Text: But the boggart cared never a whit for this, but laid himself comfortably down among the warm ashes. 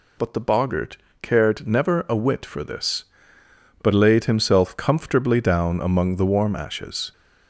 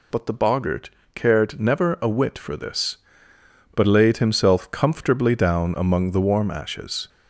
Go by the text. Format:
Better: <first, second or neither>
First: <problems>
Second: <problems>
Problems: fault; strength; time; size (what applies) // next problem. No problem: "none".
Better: neither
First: pauses between "boggart" and "cared"; slight; at 0.9 s; 0.24 s long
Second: pauses between "boggart" and "cared"; slight; at 0.8 s; 0.24 s long